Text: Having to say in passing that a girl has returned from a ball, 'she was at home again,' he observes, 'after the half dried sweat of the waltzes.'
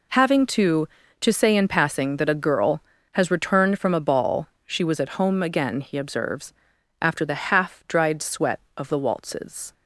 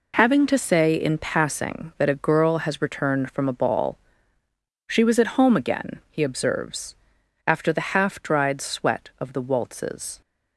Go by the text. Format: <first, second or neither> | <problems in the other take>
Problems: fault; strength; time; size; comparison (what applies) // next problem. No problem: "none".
second | says "to" twice; at 1.2 s